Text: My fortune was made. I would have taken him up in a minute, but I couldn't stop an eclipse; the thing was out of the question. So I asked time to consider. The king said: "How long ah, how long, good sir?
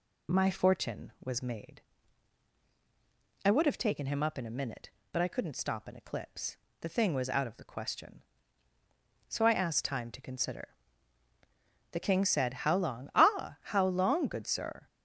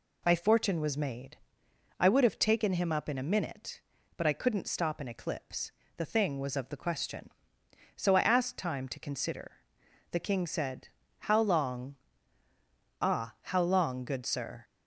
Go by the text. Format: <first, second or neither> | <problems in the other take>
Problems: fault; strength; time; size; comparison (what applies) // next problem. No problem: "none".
first | skips "out"; at 6.5 s // pauses between "long" and "ah"; at 11.9 s; 1.0 s long